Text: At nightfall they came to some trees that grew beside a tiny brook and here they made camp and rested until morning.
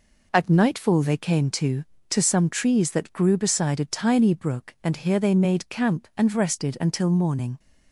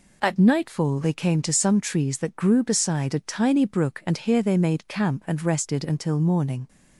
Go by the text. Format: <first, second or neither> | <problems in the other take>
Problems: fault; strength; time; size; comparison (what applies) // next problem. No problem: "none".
second | says "to" twice; at 2.1 s